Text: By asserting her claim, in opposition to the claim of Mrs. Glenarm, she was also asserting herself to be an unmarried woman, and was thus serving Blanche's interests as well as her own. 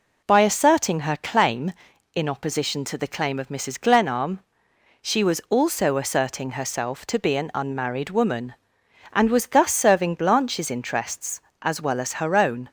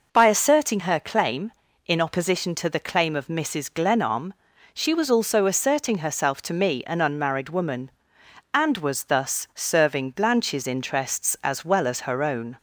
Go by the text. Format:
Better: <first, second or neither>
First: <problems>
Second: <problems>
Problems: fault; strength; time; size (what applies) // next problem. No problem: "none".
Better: first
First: none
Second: says "me" for "be"; at 6.5 s